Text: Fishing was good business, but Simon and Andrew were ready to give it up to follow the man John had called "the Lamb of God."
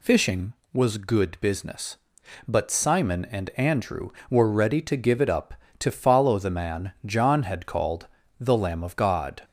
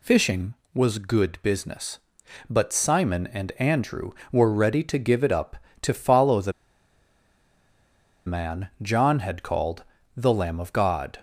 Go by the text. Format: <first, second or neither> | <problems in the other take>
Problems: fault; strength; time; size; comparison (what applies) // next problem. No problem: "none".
first | pauses between "the" and "man"; strong; at 6.5 s; 1.7 s long // pauses between "called" and "the"; slight; at 9.8 s; 0.34 s long; slight in the first